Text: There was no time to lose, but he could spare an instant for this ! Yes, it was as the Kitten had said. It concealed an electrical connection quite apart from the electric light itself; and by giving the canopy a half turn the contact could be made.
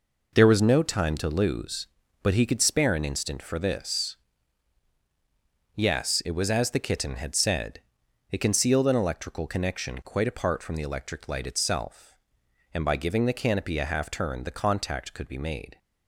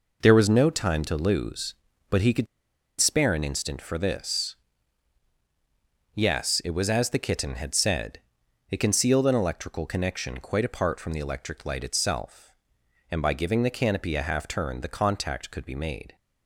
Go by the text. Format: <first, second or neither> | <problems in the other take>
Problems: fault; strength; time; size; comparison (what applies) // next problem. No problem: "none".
first | pauses between "could" and "spare"; noticeable; at 2.4 s; 0.54 s long